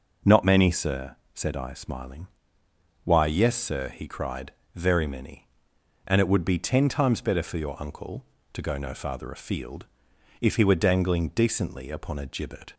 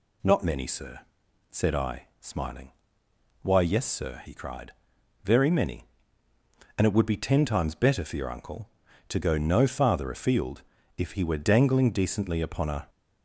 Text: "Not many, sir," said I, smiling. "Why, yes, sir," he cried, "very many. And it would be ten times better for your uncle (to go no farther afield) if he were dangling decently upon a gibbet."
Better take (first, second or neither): first